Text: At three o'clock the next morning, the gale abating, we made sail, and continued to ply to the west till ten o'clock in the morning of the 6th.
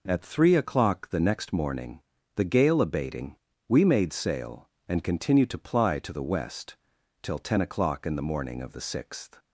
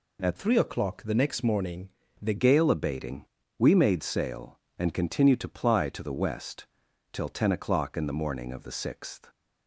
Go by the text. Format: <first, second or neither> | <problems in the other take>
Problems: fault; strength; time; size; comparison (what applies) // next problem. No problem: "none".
first | changes voice from "three" to "the"; from 0.3 to 2.3 s; 2.0 s long // pauses between "west" and "till"; noticeable; at 6.6 s; 0.48 s long; noticeable in the first